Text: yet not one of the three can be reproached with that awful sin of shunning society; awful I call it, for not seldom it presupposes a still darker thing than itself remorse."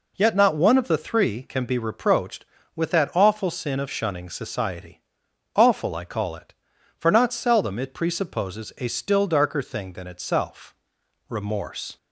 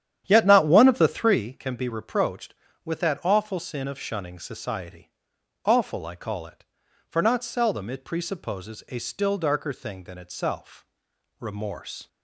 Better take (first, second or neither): first